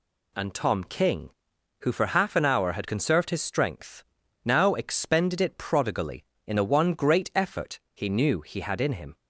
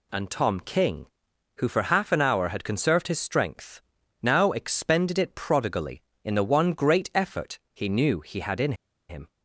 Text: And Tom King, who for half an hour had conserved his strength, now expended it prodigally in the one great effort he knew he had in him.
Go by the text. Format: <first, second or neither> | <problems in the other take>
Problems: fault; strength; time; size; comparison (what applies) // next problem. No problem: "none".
first | pauses between "in" and "him"; slight; at 8.7 s; 0.36 s long